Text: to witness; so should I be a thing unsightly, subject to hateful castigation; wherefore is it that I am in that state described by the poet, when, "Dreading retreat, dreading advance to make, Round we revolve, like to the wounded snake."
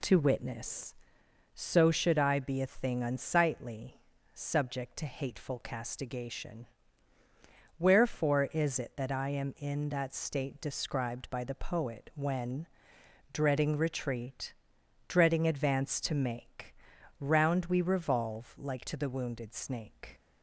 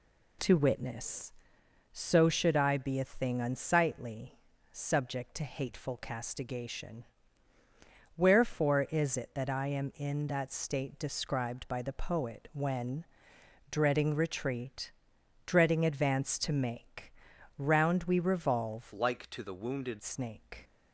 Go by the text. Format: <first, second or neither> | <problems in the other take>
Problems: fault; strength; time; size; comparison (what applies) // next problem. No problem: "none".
first | changes voice from "like" to "wounded"; from 18.9 to 20.0 s; 1.1 s long